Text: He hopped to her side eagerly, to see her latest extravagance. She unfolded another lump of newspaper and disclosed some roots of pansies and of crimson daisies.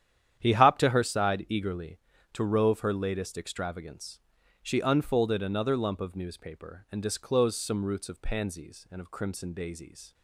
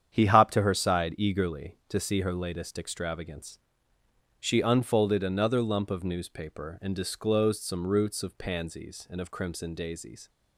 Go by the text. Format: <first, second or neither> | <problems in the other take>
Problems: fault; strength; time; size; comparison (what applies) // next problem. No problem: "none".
second | starts louder than the rest; strong; until 1.4 s; 10 dB; strong in the second // says "rove" for "see"; at 2.4 s